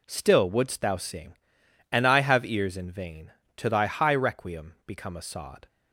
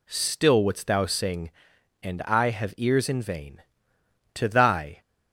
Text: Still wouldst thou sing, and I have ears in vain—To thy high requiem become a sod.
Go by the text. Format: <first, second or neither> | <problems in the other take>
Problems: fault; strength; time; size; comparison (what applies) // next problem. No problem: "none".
first | stops before "high requiem become a sod"; at 5.0 s